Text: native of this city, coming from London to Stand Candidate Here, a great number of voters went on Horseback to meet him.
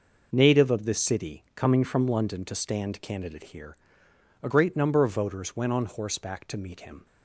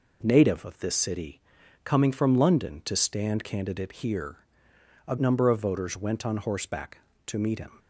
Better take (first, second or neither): first